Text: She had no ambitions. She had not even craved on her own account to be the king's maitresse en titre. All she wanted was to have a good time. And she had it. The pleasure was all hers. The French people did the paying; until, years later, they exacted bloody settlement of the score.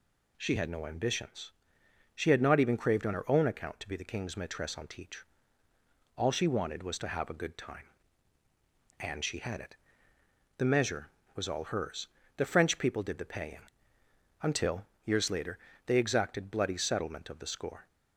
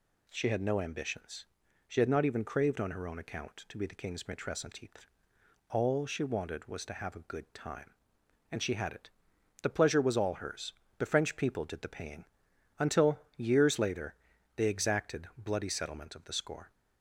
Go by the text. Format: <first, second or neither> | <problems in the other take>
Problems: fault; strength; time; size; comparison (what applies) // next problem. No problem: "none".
second | says "measure" for "pleasure"; at 10.6 s